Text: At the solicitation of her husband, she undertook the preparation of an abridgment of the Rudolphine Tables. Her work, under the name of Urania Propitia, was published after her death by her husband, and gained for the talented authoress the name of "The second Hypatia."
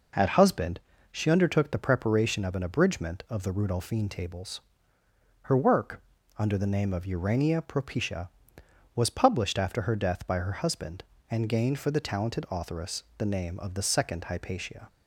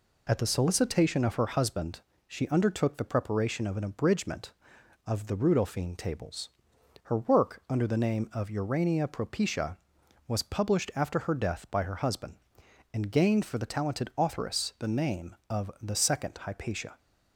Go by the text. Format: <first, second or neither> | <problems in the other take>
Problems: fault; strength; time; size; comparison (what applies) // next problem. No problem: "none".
second | skips "the solicitation of her"; at 0.3 s // pauses between "authoress" and "the"; slight; at 13.0 s; 0.16 s long